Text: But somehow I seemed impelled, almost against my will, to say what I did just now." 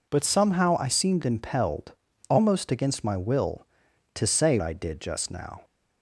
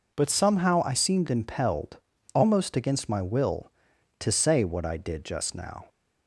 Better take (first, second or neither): second